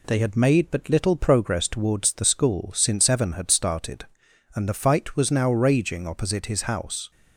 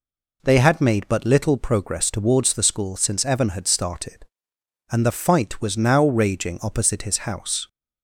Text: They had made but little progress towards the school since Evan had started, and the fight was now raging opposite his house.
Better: neither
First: none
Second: none

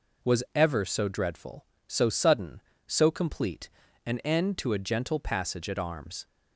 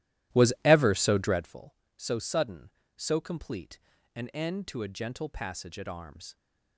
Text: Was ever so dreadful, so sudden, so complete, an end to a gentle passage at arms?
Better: first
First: none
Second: starts louder than the rest; strong; until 1.6 s; 14.5 dB

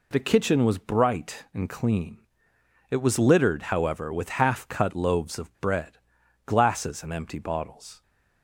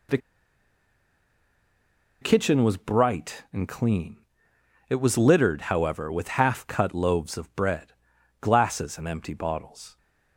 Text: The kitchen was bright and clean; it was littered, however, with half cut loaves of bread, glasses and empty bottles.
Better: first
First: none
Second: pauses between "The" and "kitchen"; strong; at 0.1 s; 2.0 s long

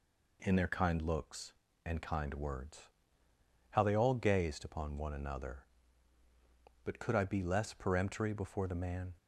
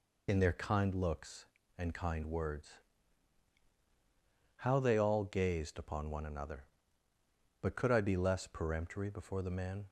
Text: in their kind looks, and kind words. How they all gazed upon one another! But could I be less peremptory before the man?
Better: first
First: none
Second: loses the start of "in"; at 0.2 s; 25 ms

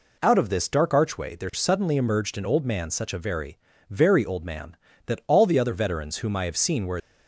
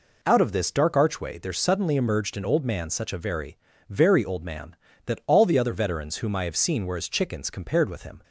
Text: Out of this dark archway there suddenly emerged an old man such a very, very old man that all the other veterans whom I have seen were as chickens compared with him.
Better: second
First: stops before "as chickens compared with him"; at 6.9 s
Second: none

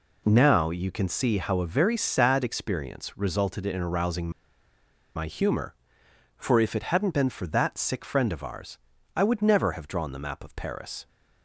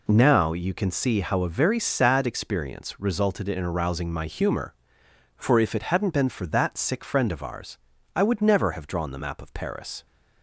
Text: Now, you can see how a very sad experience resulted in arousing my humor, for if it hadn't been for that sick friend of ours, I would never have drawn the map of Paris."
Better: second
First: pauses between "arousing" and "my"; noticeable; at 4.3 s; 0.85 s long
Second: none

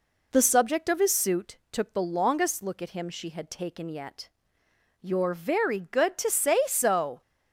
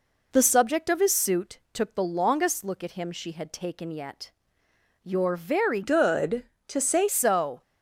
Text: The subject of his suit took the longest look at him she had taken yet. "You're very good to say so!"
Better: first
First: none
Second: changes voice from "good" to "say"; from 5.8 to 7.0 s; 1.2 s long

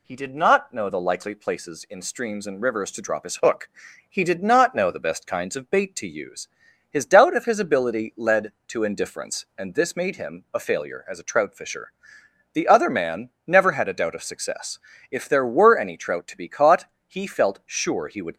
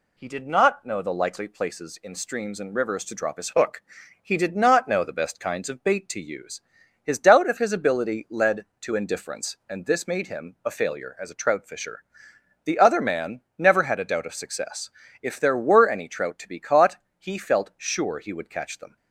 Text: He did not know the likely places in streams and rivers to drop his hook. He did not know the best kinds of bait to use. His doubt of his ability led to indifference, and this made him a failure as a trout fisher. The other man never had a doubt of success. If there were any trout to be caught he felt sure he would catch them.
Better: second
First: pauses between "man" and "never"; slight; at 13.3 s; 0.16 s long // pauses between "caught" and "he"; slight; at 16.8 s; 0.22 s long // stops before "catch them"; at 18.3 s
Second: pauses between "man" and "never"; slight; at 13.4 s; 0.16 s long // pauses between "caught" and "he"; slight; at 16.9 s; 0.22 s long

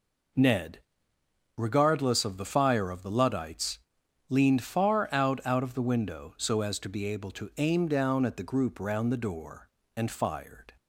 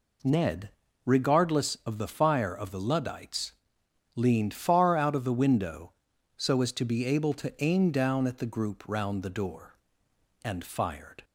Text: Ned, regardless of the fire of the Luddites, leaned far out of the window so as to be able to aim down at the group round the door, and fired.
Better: second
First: says "out" twice; at 5.4 s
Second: none

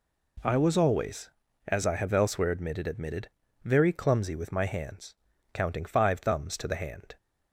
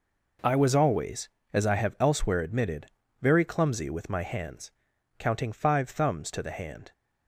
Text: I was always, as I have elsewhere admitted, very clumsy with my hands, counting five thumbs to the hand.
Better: second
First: says "admitted" twice; at 2.8 s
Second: none

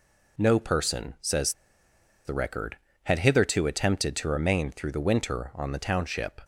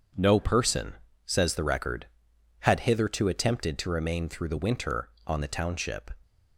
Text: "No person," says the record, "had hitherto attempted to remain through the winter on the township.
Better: second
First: pauses between "says" and "the"; noticeable; at 1.5 s; 0.72 s long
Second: none

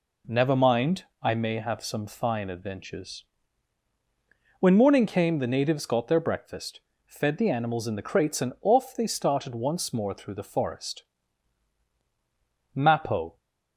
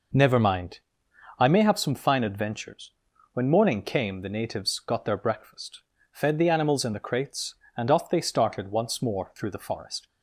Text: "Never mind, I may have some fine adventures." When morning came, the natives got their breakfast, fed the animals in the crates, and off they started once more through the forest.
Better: second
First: goes on to say "Mappo"; noticeable; from 12.7 s on; 0.62 s long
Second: none

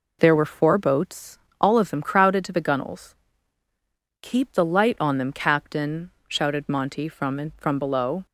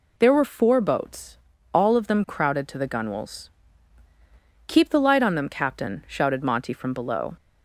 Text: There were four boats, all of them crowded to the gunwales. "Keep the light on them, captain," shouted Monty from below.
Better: second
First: says "from" twice; at 7.5 s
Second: none

